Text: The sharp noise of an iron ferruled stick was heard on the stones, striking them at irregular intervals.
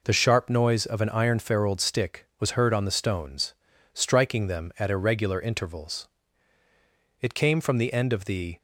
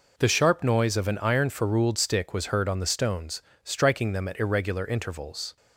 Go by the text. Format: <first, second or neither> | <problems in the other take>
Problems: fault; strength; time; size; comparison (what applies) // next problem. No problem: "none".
second | goes on to say "It came from the end of the"; from 7.2 s on; 1.3 s long